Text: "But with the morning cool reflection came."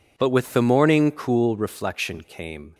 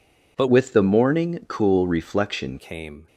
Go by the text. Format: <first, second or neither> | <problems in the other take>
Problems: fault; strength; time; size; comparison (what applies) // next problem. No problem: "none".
first | changes voice from "with" to "reflection"; from 0.4 to 2.5 s; 2.1 s long